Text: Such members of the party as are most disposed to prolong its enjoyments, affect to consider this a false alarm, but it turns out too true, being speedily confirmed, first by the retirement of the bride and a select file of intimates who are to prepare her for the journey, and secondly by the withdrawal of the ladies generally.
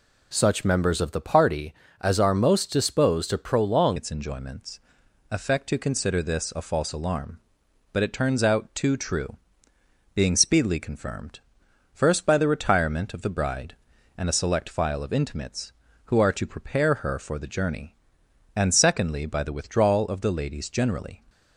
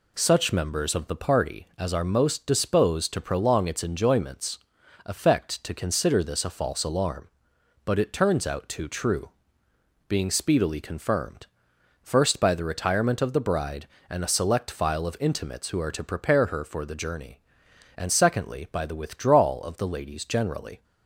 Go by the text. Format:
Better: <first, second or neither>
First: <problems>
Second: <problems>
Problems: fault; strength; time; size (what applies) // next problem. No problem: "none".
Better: second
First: changes voice at "its"; from 3.9 s on; 17.3 s long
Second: none